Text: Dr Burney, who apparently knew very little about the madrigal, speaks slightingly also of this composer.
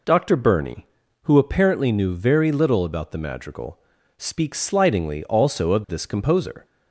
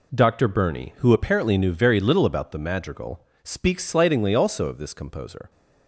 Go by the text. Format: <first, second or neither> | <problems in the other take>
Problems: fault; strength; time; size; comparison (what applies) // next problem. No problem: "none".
neither | none